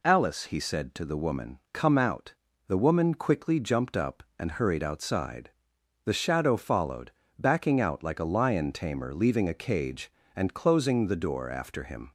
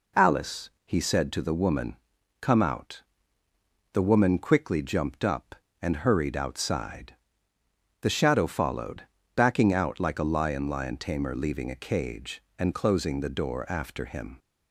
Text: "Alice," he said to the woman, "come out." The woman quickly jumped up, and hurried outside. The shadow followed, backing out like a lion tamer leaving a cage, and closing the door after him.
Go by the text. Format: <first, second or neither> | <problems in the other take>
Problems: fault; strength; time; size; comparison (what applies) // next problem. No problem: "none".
first | says "lion" twice; at 10.6 s